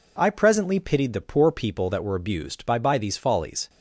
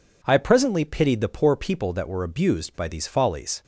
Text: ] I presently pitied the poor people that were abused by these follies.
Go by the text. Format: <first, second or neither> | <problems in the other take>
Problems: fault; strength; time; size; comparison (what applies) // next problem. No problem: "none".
second | says "by" twice; at 2.7 s